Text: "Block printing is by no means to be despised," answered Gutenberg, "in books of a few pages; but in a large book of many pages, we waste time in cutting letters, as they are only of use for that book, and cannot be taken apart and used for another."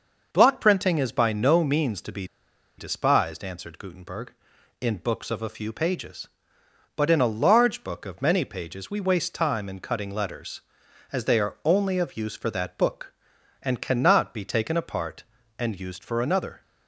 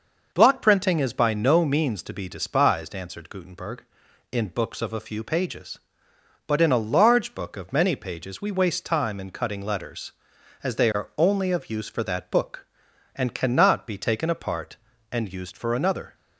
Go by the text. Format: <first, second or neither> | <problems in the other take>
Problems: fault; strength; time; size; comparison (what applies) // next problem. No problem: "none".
second | pauses between "be" and "despised"; noticeable; at 2.2 s; 0.53 s long